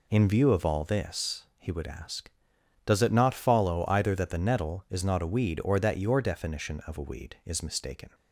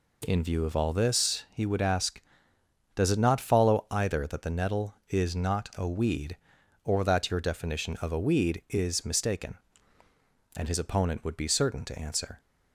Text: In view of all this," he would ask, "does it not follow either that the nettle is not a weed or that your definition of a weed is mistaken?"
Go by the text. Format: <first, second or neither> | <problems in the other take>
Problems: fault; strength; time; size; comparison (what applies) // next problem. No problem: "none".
first | goes on to say "And his opponent would be certain to answer"; strong; from 10.5 s on; 1.8 s long